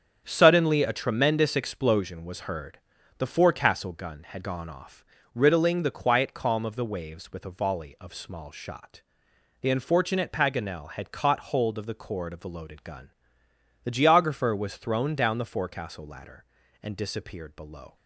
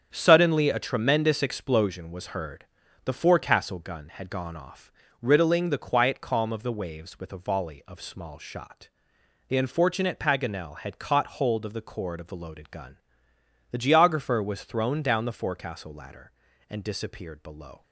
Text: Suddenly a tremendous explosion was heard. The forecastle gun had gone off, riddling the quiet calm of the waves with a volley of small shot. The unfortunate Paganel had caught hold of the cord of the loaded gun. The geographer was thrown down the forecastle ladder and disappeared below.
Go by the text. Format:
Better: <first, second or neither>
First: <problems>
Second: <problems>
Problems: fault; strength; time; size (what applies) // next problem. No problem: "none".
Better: neither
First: starts louder than the rest; strong; until 1.2 s; 7.5 dB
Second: starts louder than the rest; strong; until 1.1 s; 8 dB